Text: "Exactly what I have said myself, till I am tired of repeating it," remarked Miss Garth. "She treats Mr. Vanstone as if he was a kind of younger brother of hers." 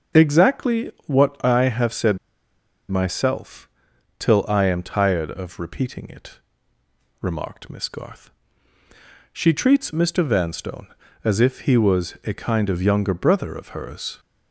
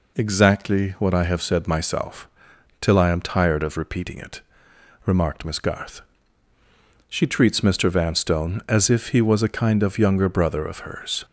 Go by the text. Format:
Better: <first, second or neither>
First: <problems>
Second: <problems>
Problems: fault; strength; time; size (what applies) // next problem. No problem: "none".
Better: second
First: starts louder than the rest; until 1.3 s; 6.5 dB // pauses between "Exactly" and "what"; slight; at 0.9 s; 0.16 s long // pauses between "said" and "myself"; noticeable; at 2.1 s; 0.71 s long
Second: none